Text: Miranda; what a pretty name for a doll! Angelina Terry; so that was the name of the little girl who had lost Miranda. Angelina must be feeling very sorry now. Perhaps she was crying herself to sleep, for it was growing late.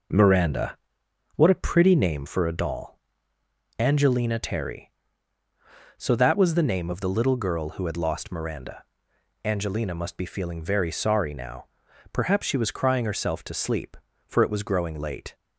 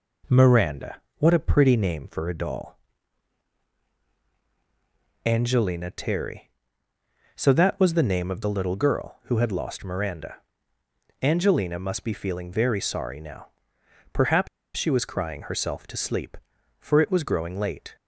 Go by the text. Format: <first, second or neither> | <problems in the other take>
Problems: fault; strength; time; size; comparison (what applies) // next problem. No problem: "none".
first | pauses between "Perhaps" and "she"; slight; at 14.4 s; 0.29 s long